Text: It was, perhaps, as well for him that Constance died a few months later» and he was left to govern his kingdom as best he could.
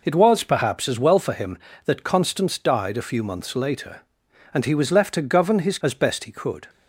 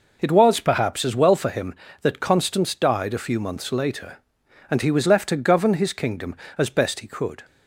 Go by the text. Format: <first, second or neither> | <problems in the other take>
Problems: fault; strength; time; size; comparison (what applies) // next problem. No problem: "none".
second | skips "kingdom"; at 5.7 s